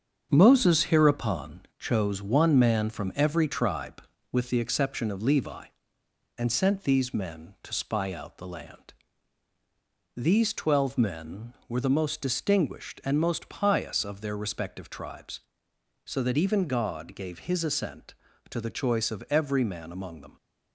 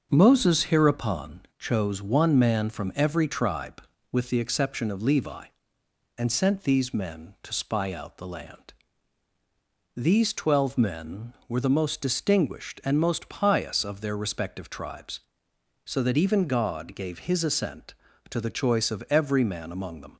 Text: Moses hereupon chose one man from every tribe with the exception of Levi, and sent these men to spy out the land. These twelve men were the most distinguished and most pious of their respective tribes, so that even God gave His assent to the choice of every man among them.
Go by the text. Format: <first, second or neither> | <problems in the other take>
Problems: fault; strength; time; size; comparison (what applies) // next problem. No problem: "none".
second | gets quieter; noticeable; throughout; 6 dB // starts louder than the rest; until 1.3 s; 7 dB; also in the second